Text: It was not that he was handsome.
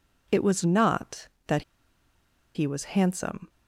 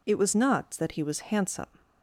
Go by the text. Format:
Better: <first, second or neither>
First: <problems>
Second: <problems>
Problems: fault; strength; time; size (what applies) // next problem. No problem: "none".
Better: second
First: pauses between "that" and "he"; noticeable; at 1.6 s; 0.92 s long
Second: none